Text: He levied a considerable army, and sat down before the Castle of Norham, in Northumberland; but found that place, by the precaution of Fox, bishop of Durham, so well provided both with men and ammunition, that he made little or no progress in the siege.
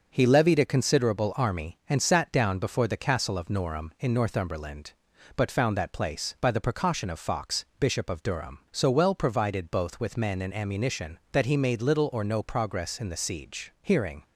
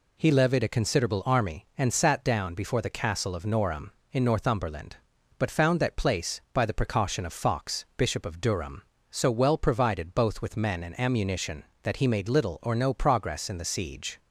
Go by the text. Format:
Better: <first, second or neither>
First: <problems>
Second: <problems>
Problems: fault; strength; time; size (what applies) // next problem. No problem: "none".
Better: second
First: goes on to say "Hearing"; slight; from 13.8 s on; 0.42 s long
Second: none